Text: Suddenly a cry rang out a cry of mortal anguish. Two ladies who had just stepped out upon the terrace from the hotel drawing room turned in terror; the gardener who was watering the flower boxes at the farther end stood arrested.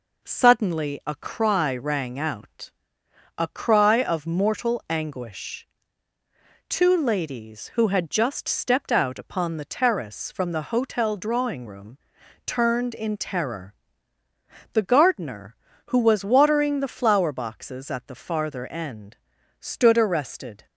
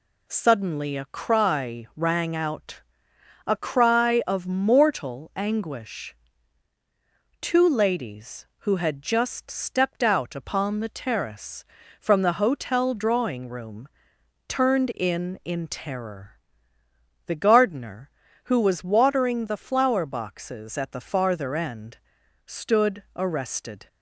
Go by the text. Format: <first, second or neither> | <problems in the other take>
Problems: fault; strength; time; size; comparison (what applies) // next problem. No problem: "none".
first | pauses between "out" and "a"; noticeable; at 2.8 s; 0.64 s long; noticeable in the first // pauses between "room" and "turned"; noticeable; at 13.8 s; 0.60 s long; noticeable in the first // says "in" twice; at 15.4 s // pauses between "end" and "stood"; noticeable; at 21.9 s; 0.48 s long; also in the first